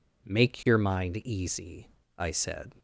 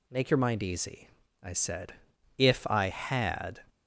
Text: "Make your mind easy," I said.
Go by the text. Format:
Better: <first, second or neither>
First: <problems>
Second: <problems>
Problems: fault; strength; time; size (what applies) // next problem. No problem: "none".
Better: first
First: none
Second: goes on to say "If I had"; noticeable; from 2.3 s on; 1.2 s long